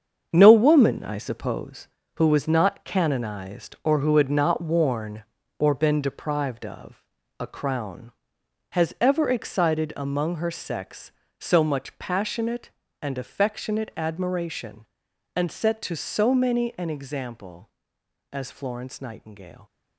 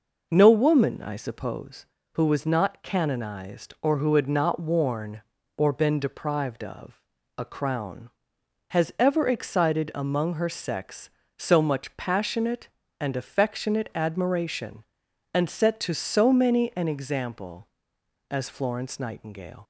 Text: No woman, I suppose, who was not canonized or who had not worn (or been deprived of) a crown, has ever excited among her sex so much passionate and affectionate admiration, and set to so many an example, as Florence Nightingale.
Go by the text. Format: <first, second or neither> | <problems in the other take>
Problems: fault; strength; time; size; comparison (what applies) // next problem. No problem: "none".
second | gets quieter; strong; throughout; 8.5 dB